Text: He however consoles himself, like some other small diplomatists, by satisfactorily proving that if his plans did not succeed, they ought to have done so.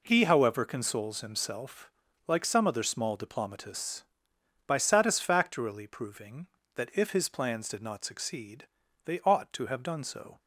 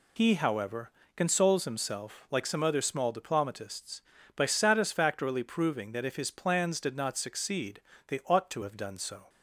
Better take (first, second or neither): first